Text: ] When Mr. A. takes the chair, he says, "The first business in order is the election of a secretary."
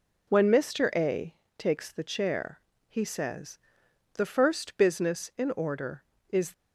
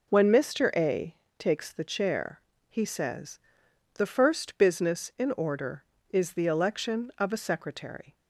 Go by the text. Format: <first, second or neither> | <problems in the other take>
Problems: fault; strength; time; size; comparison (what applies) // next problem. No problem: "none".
second | pauses between "A" and "takes"; slight; at 1.3 s; 0.22 s long; slight in the second // stops before "the election of a secretary"; at 6.5 s